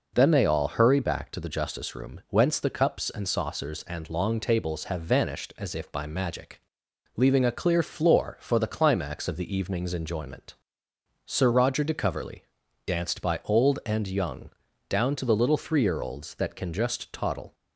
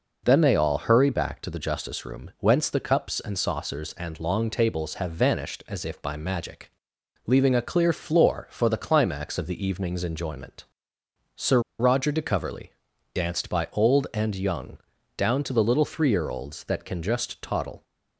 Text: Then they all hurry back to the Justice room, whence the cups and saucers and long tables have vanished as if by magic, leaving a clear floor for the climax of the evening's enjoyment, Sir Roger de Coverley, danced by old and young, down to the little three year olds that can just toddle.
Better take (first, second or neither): first